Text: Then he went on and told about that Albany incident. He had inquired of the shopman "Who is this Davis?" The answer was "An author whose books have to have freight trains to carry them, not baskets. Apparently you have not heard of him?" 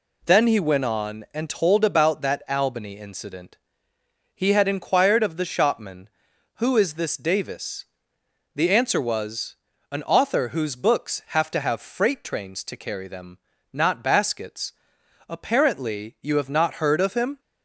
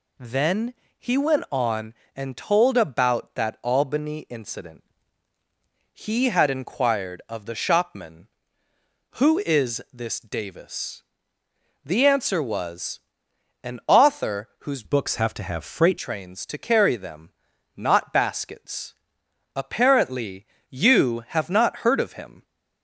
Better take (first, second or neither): first